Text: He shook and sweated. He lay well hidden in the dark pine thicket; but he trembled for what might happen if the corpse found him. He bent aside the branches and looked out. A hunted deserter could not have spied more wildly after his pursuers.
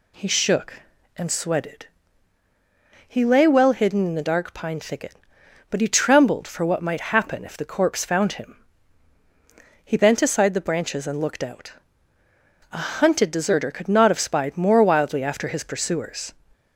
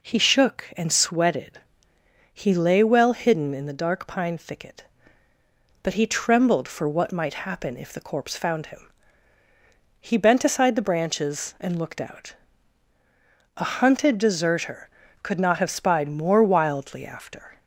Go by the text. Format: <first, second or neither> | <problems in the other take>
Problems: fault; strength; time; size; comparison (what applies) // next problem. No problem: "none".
first | stops before "his pursuers"; at 17.5 s